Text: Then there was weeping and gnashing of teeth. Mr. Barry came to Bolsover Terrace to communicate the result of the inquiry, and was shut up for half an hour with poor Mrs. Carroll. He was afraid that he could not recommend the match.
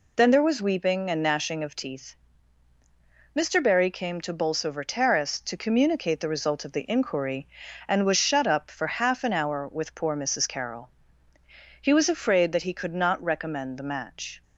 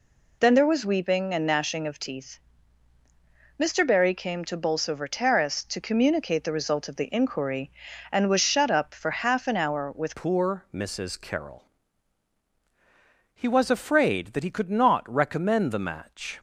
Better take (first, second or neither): first